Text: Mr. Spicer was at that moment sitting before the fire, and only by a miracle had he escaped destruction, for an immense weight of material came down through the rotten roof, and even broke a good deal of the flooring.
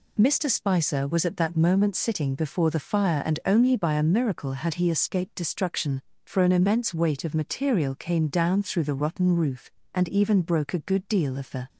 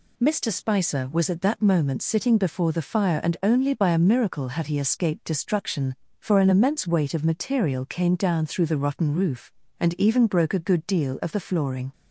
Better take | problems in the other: second | stops before "flooring"; at 11.6 s

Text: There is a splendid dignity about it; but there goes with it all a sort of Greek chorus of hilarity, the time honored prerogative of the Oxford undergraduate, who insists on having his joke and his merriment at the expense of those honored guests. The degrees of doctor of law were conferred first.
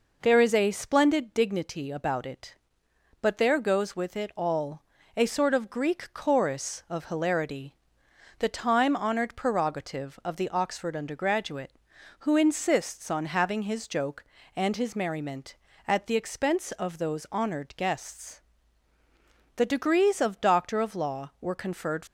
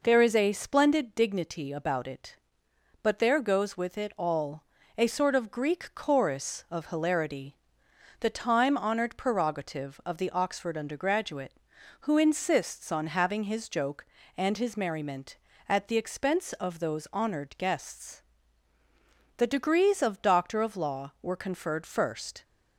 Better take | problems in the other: second | pauses between "all" and "a"; slight; at 4.8 s; 0.34 s long; slight in the second // stops before "first"; at 22.0 s

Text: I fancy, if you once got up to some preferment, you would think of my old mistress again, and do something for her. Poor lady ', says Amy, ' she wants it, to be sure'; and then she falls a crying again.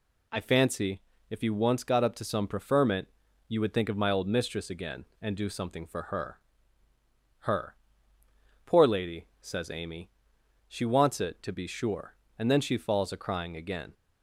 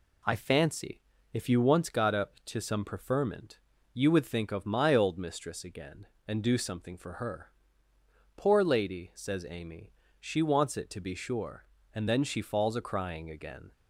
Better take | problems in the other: second | says "her" twice; at 7.4 s

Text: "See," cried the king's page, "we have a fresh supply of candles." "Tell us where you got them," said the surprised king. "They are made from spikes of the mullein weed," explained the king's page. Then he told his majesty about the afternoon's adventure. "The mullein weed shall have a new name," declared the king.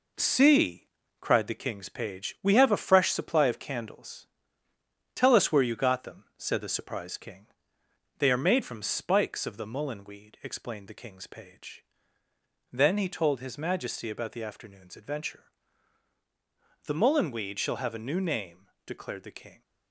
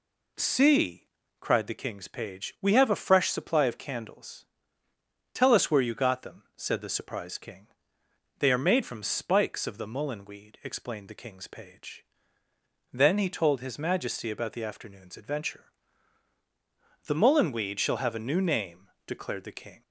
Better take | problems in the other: second | gets quieter; throughout; 6.5 dB

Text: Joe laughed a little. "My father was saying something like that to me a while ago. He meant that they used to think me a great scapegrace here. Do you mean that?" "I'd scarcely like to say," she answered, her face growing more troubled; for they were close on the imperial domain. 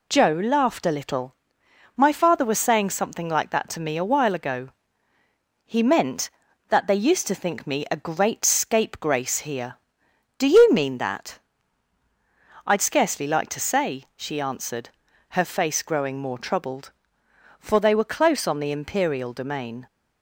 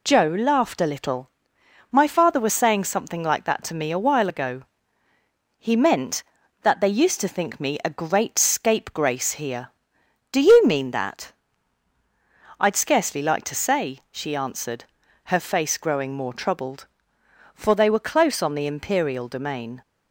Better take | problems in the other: neither | none

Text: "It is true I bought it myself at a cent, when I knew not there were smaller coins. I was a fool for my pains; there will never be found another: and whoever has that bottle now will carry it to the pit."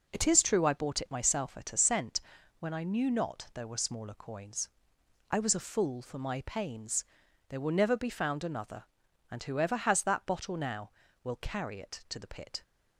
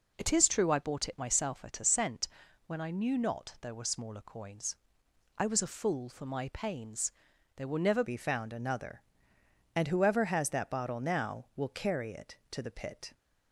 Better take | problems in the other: first | changes voice at "be"; from 8.0 s on; 5.1 s long

